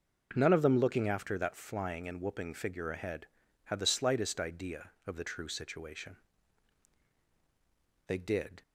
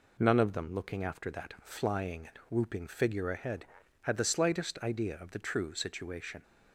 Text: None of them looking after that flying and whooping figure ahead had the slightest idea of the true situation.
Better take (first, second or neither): second